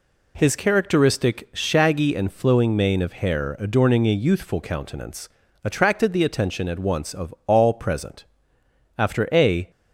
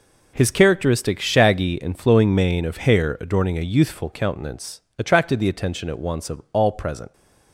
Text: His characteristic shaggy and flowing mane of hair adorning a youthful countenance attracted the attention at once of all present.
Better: second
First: pauses between "countenance" and "attracted"; slight; at 5.3 s; 0.34 s long // pauses between "of" and "all"; slight; at 7.3 s; 0.20 s long // goes on to say "After a"; noticeable; from 8.9 s on; 0.72 s long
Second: pauses between "countenance" and "attracted"; slight; at 4.8 s; 0.18 s long

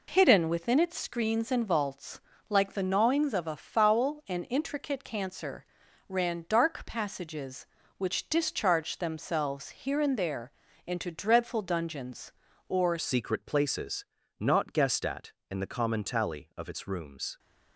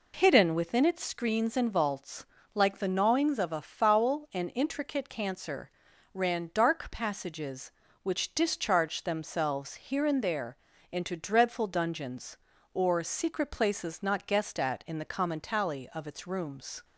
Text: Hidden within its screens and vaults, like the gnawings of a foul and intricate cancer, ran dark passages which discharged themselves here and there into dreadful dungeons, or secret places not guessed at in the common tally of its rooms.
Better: second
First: pauses between "there" and "into"; slight; at 10.5 s; 0.36 s long // changes voice at "secret"; from 12.9 s on; 4.4 s long // pauses between "places" and "not"; slight; at 14.0 s; 0.34 s long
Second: pauses between "there" and "into"; slight; at 10.5 s; 0.36 s long

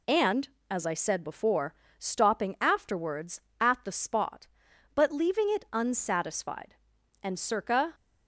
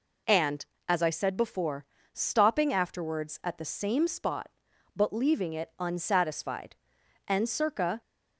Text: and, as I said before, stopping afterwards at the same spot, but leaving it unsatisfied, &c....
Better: second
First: skips "same"; at 3.9 s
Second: none

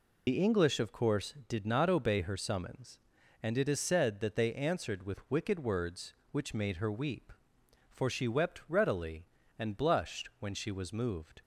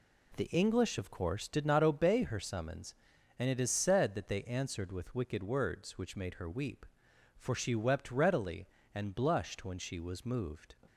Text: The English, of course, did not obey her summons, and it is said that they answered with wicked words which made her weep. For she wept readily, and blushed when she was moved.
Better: second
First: loses the start of "The"; at 0.2 s; 90 ms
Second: none

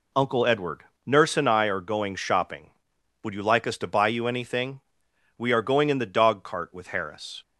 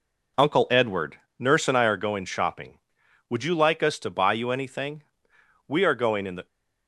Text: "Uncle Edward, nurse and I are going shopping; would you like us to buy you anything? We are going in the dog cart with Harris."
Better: first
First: none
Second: stops before "dog cart with Harris"; at 6.4 s

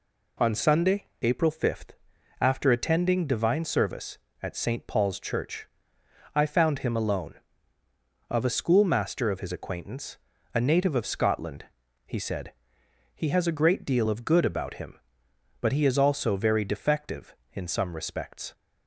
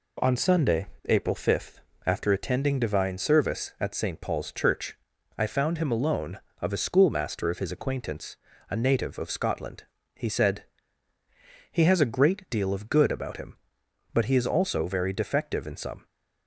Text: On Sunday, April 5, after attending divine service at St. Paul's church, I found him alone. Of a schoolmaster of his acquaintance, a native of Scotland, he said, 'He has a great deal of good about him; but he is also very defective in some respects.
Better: first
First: none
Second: stops before "respects"; at 16.0 s

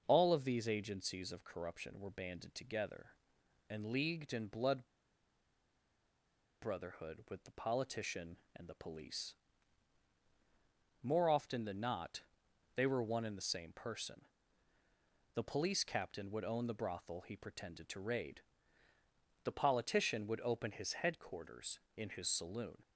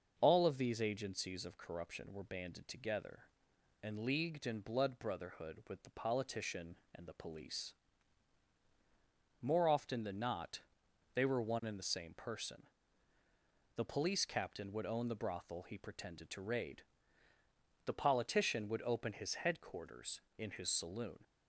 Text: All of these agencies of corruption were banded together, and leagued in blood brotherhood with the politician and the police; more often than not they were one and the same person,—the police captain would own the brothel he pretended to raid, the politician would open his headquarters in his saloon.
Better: second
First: pauses between "blood" and "brotherhood"; strong; at 4.8 s; 1.7 s long // pauses between "not" and "they"; noticeable; at 12.2 s; 0.54 s long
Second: pauses between "not" and "they"; noticeable; at 10.6 s; 0.54 s long

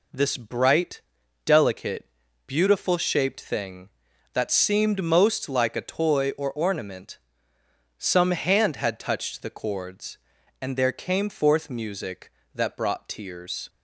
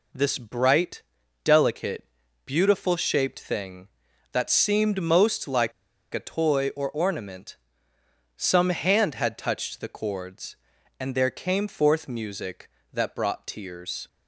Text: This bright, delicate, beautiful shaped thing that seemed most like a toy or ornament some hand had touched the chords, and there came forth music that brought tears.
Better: first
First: pauses between "ornament" and "some"; noticeable; at 7.1 s; 0.80 s long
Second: pauses between "like" and "a"; at 5.7 s; 0.41 s long // pauses between "ornament" and "some"; noticeable; at 7.5 s; 0.80 s long

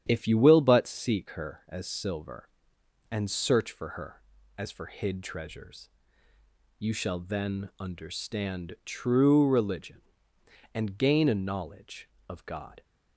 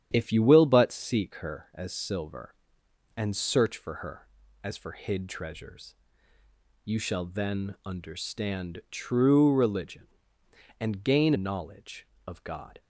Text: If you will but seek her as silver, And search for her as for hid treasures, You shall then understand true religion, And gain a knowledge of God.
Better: first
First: starts louder than the rest; strong; until 1.0 s; 9.5 dB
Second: starts louder than the rest; strong; until 1.1 s; 9.5 dB // skips "a"; at 11.3 s

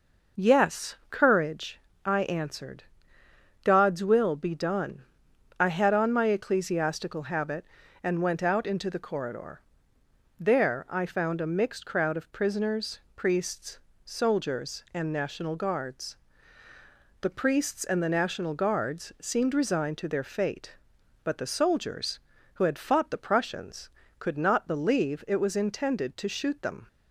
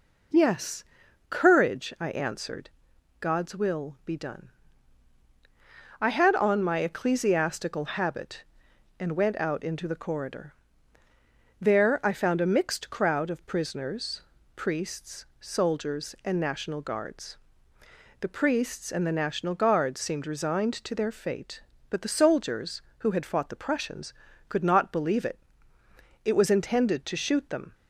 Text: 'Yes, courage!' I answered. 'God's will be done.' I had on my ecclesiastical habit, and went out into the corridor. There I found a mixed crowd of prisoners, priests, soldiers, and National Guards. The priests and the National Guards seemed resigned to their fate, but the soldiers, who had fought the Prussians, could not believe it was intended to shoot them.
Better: first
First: none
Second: says "it" twice; at 26.2 s

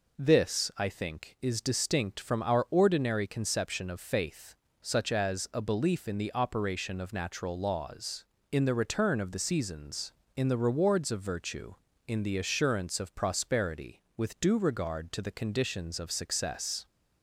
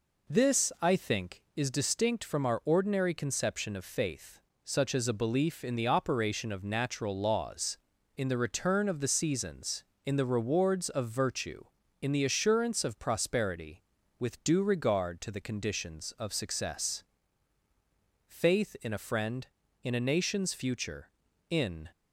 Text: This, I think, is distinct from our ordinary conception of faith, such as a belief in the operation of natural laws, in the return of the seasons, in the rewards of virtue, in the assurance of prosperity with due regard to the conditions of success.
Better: first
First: none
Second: goes on to say "Faith in a friend in a nation's future in"; strong; from 18.2 s on; 3.6 s long

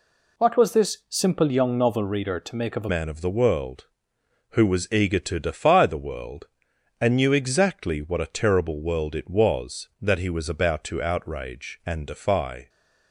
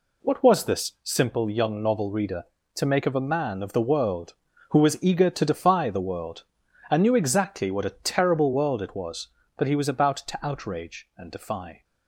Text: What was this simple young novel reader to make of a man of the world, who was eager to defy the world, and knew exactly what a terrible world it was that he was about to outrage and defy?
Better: second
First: changes voice at "man"; from 2.8 s on; 9.8 s long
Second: none

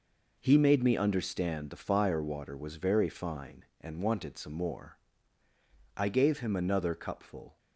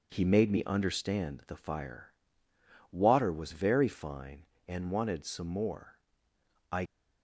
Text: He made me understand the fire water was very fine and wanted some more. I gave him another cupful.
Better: first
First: none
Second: pauses between "fire" and "water"; noticeable; at 2.1 s; 0.80 s long // stops before "gave him another cupful"; at 6.8 s

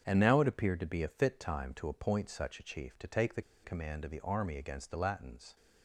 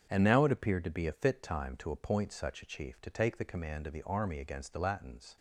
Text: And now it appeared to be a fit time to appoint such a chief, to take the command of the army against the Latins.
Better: second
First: starts louder than the rest; strong; until 1.0 s; 7 dB // pauses between "the" and "command"; slight; at 3.4 s; 0.21 s long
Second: starts louder than the rest; strong; until 1.1 s; 7 dB

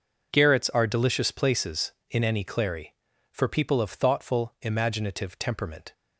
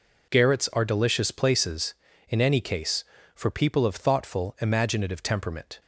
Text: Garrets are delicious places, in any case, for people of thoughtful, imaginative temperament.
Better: second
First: says "clary" for "case"; at 2.4 s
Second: none

